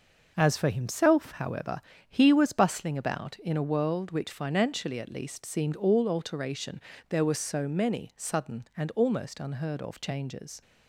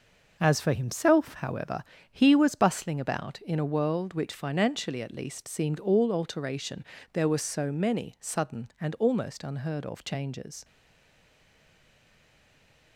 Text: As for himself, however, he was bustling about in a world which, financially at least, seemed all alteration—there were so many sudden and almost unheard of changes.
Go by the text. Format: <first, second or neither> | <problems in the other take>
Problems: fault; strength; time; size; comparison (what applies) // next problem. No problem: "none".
first | stays silent after the last word; from 10.6 s on; 2.3 s long